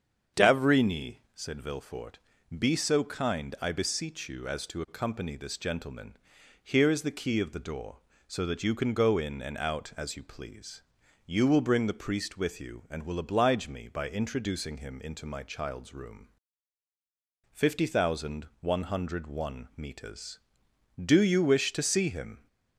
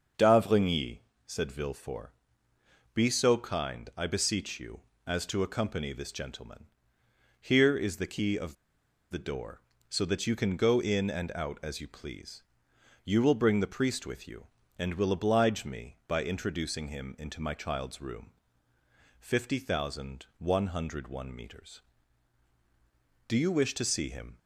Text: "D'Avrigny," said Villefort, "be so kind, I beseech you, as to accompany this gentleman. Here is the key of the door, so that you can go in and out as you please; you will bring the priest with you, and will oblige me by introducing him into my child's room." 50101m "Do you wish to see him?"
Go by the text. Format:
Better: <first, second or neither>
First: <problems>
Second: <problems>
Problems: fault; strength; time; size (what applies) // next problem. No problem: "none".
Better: first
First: starts louder than the rest; strong; until 1.5 s; 7.5 dB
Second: starts louder than the rest; until 1.4 s; 6.5 dB // pauses between "of" and "the"; noticeable; at 8.5 s; 0.56 s long